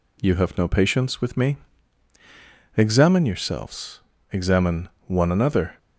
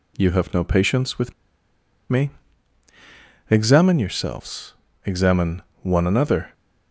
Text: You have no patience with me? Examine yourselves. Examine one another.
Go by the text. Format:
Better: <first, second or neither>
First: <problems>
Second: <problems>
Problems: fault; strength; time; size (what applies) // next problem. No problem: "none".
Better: first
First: pauses between "Examine" and "one"; slight; at 4.8 s; 0.20 s long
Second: pauses between "with" and "me"; noticeable; at 1.3 s; 0.77 s long // pauses between "Examine" and "one"; slight; at 5.6 s; 0.22 s long